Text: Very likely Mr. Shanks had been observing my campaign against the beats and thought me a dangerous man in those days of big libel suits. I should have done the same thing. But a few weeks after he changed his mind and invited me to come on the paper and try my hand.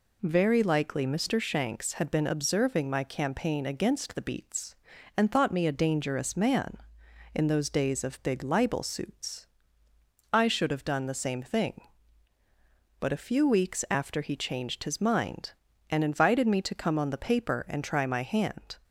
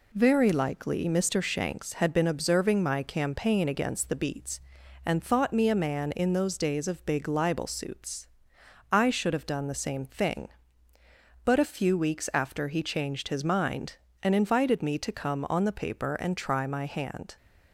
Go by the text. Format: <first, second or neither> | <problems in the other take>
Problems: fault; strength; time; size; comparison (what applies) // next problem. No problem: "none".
first | skips "dangerous"; at 5.7 s